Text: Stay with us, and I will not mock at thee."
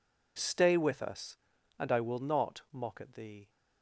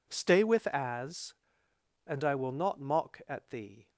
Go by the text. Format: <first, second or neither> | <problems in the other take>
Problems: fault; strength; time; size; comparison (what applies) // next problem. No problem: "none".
first | says "as" for "us"; at 0.6 s